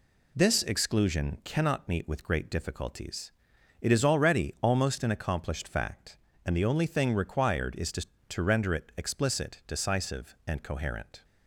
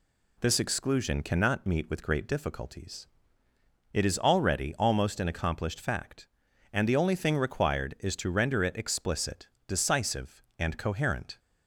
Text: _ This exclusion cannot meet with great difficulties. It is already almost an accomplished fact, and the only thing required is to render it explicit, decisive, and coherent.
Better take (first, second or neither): second